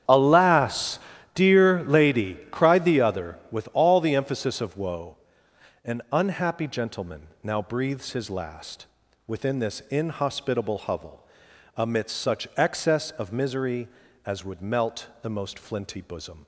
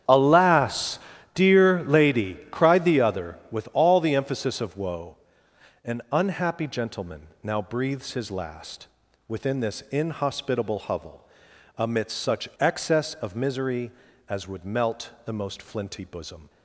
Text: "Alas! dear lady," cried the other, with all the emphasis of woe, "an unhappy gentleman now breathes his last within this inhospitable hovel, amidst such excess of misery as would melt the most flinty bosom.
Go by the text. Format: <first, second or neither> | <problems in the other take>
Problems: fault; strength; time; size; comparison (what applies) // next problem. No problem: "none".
neither | starts louder than the rest; strong; the same in both // pauses between "gentleman" and "now"; slight; the same in both // pauses between "last" and "within"; the same in both